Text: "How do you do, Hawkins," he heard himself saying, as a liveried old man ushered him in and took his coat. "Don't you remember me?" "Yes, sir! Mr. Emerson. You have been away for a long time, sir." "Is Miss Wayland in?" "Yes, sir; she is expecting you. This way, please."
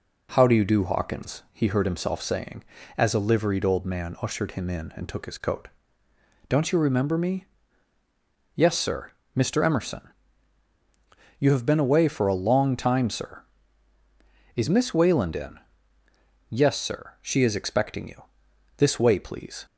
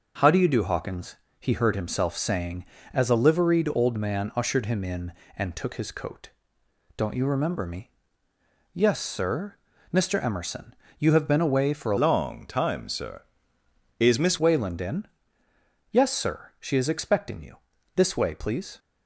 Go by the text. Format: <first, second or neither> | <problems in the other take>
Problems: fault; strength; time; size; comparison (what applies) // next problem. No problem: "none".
first | changes voice from "long" to "Miss"; from 11.9 to 14.3 s; 2.4 s long